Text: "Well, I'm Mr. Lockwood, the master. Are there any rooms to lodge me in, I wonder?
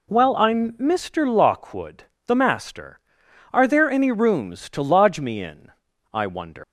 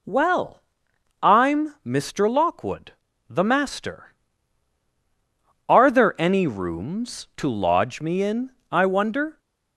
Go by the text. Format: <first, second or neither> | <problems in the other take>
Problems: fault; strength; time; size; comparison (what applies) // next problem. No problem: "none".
second | leaves "wonder" unfinished; at 6.6 s; 155 ms